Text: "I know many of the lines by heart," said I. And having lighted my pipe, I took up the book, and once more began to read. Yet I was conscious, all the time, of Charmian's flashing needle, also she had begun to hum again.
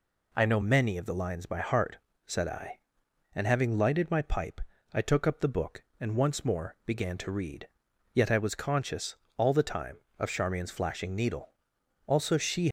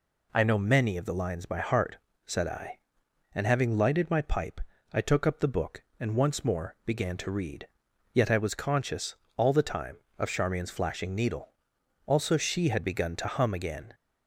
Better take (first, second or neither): second